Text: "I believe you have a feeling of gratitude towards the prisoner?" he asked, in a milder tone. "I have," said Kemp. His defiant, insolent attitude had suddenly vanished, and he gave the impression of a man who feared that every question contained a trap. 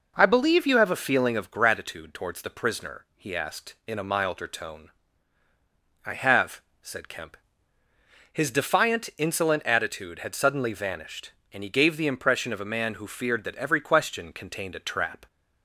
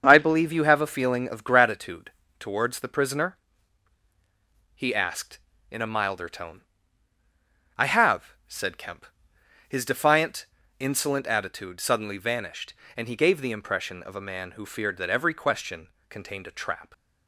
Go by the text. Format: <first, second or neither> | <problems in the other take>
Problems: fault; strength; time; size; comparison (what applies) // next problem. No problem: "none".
first | starts louder than the rest; strong; until 1.0 s; 7 dB // pauses between "gratitude" and "towards"; slight; at 2.1 s; 0.28 s long // skips "had"; at 11.8 s // pauses between "question" and "contained"; slight; at 15.8 s; 0.22 s long